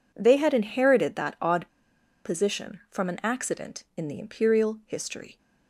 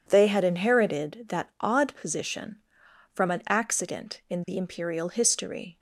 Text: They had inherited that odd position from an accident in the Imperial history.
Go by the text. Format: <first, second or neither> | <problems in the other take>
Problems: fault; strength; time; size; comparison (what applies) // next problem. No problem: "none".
second | pauses between "odd" and "position"; noticeable; at 1.6 s; 0.56 s long